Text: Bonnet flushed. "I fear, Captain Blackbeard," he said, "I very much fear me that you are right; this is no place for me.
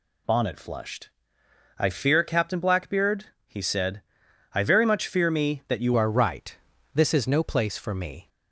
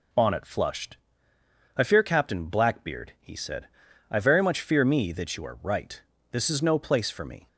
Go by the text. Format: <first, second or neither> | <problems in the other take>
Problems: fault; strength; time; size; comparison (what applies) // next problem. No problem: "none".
second | changes voice at "are"; from 5.9 s on; 2.3 s long